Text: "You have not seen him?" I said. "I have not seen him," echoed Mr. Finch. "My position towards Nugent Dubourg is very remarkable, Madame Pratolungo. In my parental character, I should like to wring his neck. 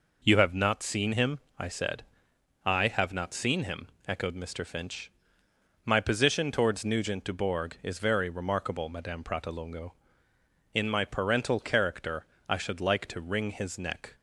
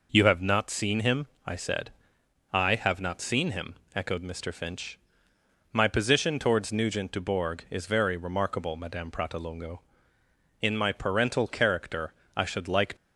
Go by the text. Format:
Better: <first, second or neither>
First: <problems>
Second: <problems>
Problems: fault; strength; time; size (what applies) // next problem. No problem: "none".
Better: first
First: none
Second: stops before "to wring his neck"; at 12.9 s